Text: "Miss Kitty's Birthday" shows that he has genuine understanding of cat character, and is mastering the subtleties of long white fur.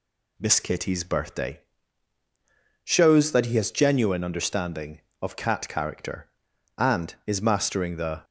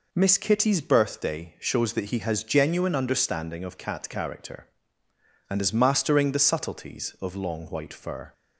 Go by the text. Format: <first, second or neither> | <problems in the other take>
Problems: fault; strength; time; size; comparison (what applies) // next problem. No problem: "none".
second | pauses between "Birthday" and "shows"; at 1.5 s; 1.2 s long // stops before "subtleties of long white fur"; at 8.2 s